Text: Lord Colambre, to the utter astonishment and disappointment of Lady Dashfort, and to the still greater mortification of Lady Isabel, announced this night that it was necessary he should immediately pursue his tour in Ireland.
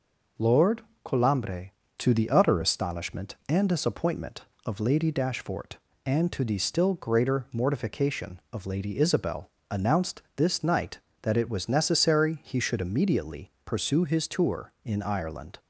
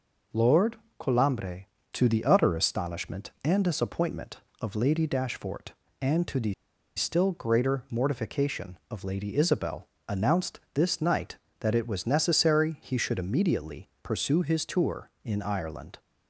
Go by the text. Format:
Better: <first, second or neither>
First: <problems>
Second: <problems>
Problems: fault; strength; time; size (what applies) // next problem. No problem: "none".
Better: first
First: pauses between "Lord" and "Colambre"; slight; at 0.8 s; 0.22 s long // pauses between "immediately" and "pursue"; slight; at 13.5 s; 0.16 s long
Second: pauses between "Lord" and "Colambre"; slight; at 0.7 s; 0.22 s long // pauses between "the" and "still"; at 6.5 s; 0.44 s long // pauses between "immediately" and "pursue"; slight; at 13.8 s; 0.16 s long